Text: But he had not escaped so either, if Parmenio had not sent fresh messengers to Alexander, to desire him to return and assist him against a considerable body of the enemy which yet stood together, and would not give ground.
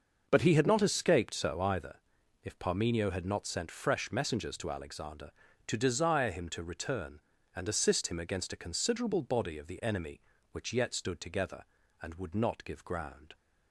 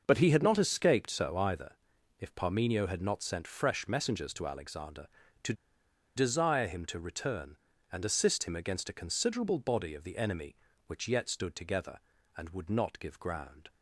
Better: first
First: starts louder than the rest; noticeable; until 1.2 s; 6 dB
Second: starts louder than the rest; noticeable; until 1.0 s; 6 dB // pauses between "to" and "desire"; noticeable; at 5.5 s; 0.62 s long

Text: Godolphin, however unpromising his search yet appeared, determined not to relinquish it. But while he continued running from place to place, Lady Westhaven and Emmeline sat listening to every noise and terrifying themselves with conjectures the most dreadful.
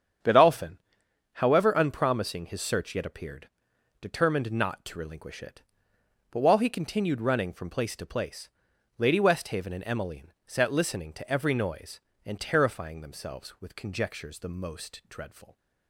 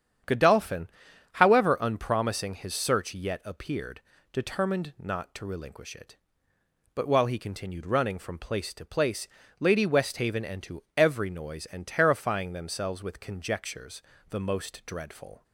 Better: first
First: starts louder than the rest; strong; until 1.8 s; 8 dB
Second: starts louder than the rest; strong; until 1.7 s; 9 dB // skips "Emmeline sat listening"; at 10.6 s // pauses between "conjectures" and "the"; slight; at 14.0 s; 0.28 s long

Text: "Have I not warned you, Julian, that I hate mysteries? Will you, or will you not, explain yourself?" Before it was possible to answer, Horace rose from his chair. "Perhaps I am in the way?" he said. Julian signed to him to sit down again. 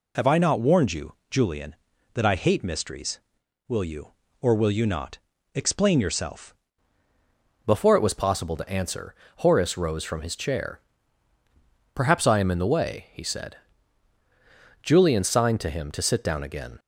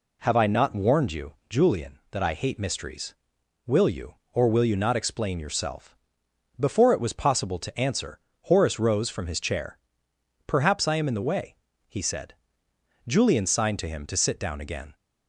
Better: second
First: changes voice at "Before"; from 7.6 s on; 9.1 s long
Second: none

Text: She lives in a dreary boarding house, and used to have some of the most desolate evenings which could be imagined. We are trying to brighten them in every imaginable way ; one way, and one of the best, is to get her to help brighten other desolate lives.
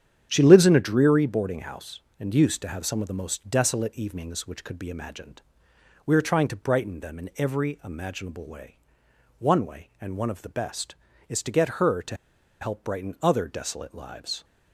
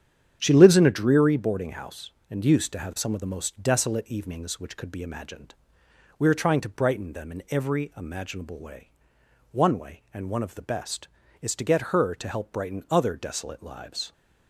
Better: second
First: starts louder than the rest; strong; until 1.3 s; 9 dB // pauses between "to" and "help"; at 12.1 s; 0.45 s long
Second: starts louder than the rest; strong; until 1.4 s; 9 dB

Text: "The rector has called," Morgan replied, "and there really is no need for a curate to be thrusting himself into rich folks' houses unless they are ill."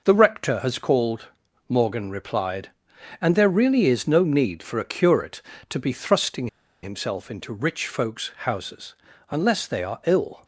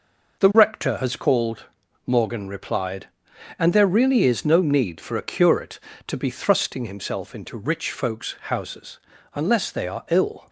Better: second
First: pauses between "thrusting" and "himself"; at 6.4 s; 0.36 s long // pauses between "houses" and "unless"; slight; at 8.9 s; 0.36 s long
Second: pauses between "houses" and "unless"; slight; at 8.9 s; 0.36 s long

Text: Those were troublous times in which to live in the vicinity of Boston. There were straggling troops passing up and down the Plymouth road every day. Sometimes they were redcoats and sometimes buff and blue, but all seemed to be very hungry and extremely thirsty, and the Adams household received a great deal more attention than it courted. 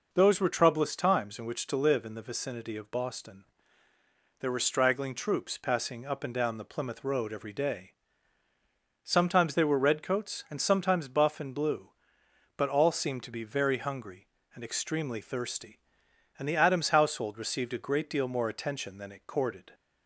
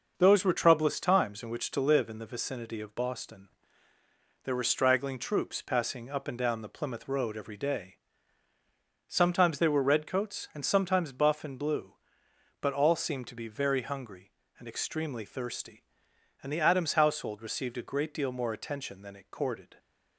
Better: first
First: none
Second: gets quieter; noticeable; throughout; 5.5 dB

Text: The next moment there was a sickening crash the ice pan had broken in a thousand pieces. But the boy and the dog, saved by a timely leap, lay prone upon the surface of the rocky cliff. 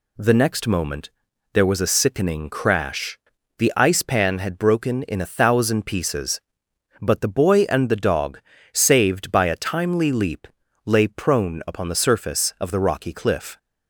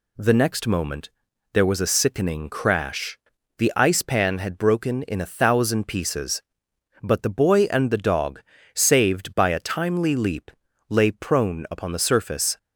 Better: first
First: pauses between "moment" and "there"; at 1.0 s; 0.42 s long // pauses between "crash" and "the"; at 3.1 s; 0.38 s long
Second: pauses between "moment" and "there"; at 1.0 s; 0.42 s long // pauses between "crash" and "the"; at 3.1 s; 0.38 s long // stops before "of the rocky cliff"; at 12.5 s

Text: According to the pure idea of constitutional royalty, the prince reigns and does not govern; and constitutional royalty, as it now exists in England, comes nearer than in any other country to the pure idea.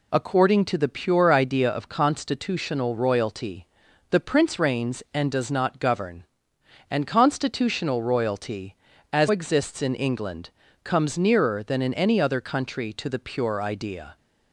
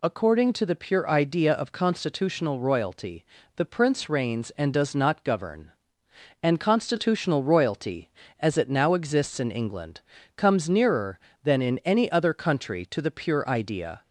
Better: second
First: skips "it now"; at 9.2 s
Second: none

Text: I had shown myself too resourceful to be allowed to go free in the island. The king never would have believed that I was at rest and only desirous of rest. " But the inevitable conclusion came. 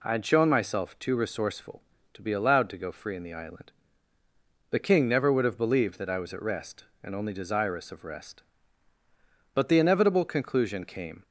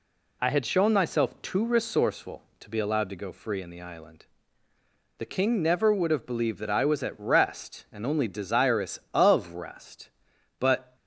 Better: first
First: none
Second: stops before "the inevitable conclusion came"; at 10.9 s

